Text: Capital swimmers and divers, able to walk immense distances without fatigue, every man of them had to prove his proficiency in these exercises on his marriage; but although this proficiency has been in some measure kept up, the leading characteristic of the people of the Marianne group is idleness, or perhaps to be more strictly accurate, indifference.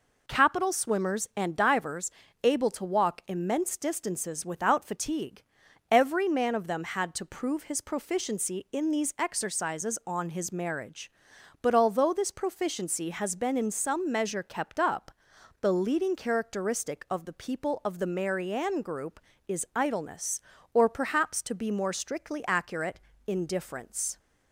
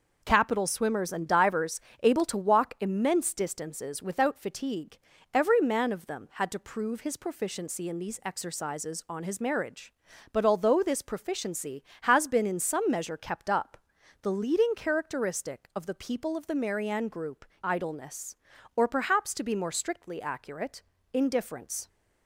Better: first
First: none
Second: skips "is"; at 17.5 s

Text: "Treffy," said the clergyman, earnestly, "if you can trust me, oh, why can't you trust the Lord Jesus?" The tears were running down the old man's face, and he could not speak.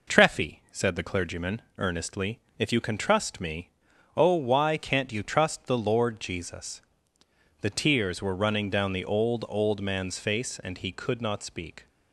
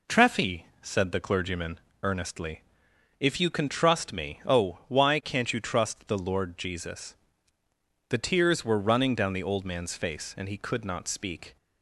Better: second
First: says "old" twice; at 9.4 s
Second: none

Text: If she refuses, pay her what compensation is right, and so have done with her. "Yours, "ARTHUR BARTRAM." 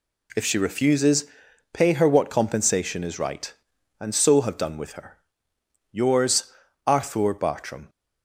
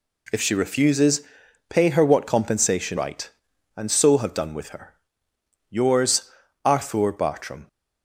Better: first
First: none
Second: skips "is"; at 2.9 s

